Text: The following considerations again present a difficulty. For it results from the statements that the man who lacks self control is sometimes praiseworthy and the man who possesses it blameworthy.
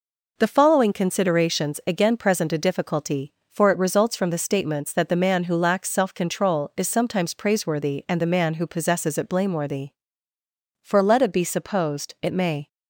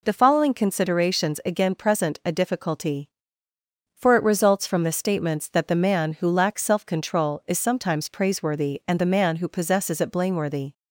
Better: second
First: goes on to say "For let it be supposed it may"; strong; from 10.8 s on; 1.8 s long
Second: none

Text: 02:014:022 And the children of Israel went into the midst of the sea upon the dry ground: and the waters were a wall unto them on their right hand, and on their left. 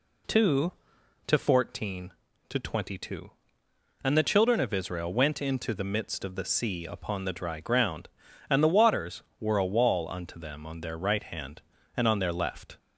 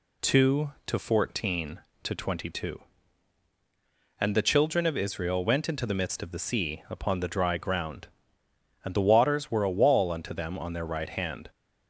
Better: first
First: none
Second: stops before "and on their left"; at 11.4 s

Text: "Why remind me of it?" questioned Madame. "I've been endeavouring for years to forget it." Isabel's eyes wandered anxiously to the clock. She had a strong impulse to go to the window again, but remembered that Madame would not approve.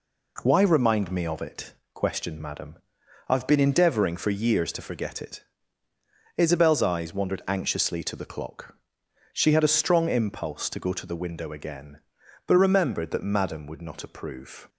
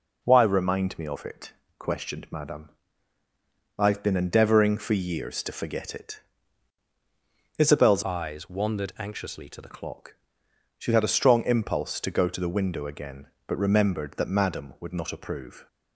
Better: first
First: none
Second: changes voice from "eyes" to "the"; from 8.0 to 9.7 s; 1.7 s long

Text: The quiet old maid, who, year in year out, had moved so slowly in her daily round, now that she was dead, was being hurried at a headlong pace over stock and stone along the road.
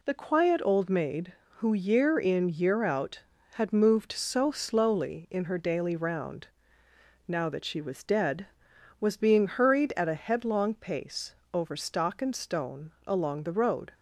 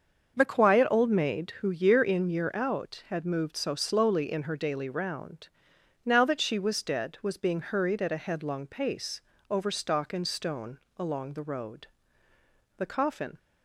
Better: first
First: pauses between "pace" and "over"; slight; at 11.3 s; 0.18 s long // pauses between "stone" and "along"; slight; at 12.8 s; 0.16 s long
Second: starts louder than the rest; until 1.3 s; 6.5 dB // pauses between "pace" and "over"; slight; at 9.2 s; 0.26 s long // pauses between "stone" and "along"; slight; at 10.7 s; 0.18 s long // goes on to say "The coffin"; from 12.7 s on; 0.60 s long

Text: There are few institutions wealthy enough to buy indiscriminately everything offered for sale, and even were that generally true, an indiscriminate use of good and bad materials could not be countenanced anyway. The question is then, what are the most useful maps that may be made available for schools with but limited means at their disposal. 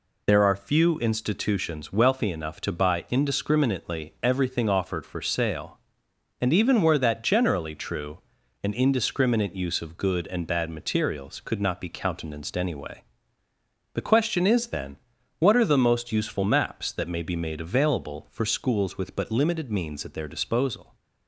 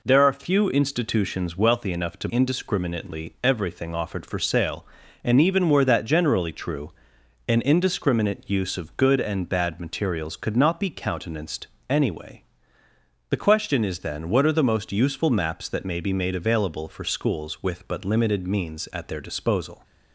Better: first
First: none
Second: skips "buy"; at 2.2 s // pauses between "countenanced" and "anyway"; slight; at 11.6 s; 0.22 s long

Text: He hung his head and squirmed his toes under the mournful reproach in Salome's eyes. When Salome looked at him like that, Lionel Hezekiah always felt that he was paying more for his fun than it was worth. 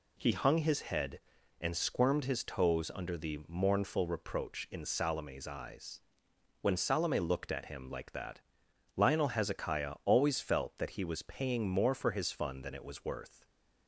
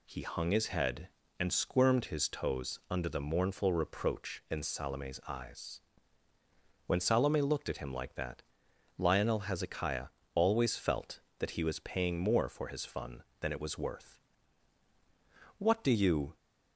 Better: first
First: none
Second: pauses between "Hezekiah" and "always"; slight; at 10.0 s; 0.28 s long // goes on to say "What do you"; noticeable; from 15.5 s on; 0.78 s long

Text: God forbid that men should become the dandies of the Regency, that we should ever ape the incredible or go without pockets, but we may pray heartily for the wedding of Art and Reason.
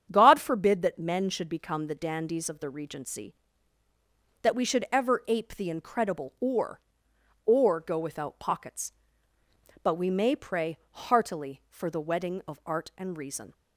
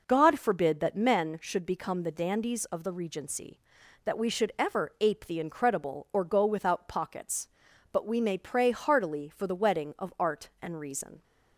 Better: second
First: starts louder than the rest; strong; until 1.1 s; 8.5 dB // says "or" twice; at 7.4 s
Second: none

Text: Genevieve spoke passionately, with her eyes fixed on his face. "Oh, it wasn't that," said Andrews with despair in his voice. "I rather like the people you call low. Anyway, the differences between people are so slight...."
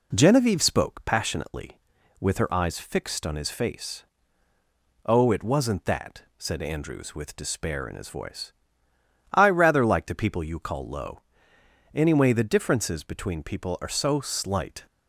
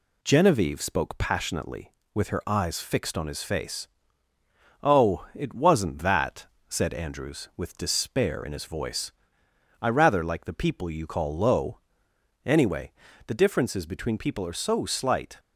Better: neither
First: none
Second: none

